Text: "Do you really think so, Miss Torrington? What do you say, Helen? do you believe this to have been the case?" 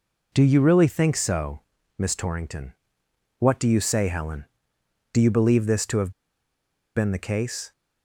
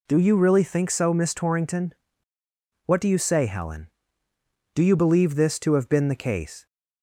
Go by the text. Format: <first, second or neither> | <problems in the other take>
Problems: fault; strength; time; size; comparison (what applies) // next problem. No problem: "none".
second | pauses between "have" and "been"; noticeable; at 6.1 s; 0.84 s long